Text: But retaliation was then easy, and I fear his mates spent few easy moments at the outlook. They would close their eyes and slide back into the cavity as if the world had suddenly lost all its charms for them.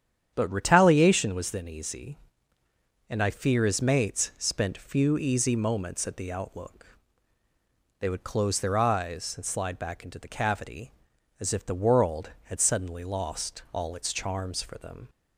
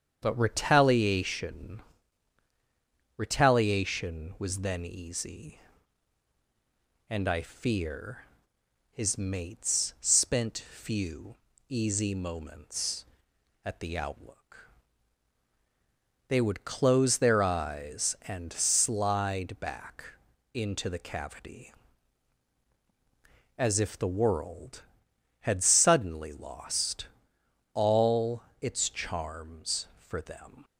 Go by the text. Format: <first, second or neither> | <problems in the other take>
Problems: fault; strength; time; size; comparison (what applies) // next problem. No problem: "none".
first | starts louder than the rest; strong; until 1.2 s; 7.5 dB; strong in the first // says "retaliation" twice; at 3.1 s // pauses between "fear" and "his"; noticeable; at 8.2 s; 0.66 s long // pauses between "few" and "easy"; slight; at 11.3 s; 0.32 s long // pauses between "back" and "into"; noticeable; at 20.0 s; 0.48 s long // pauses between "lost" and "all"; noticeable; at 27.0 s; 0.66 s long // pauses between "all" and "its"; slight; at 28.4 s; 0.18 s long